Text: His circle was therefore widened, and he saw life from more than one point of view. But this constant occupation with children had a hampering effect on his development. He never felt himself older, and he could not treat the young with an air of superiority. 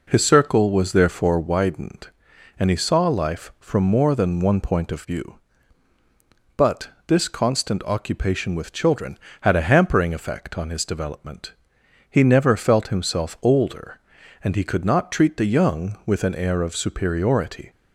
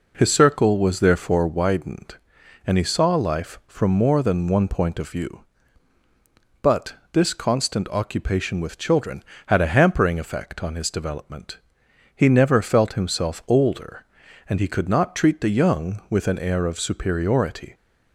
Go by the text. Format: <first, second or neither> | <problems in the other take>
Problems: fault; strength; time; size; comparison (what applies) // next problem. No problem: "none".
neither | pauses between "But" and "this"; slight; the same in both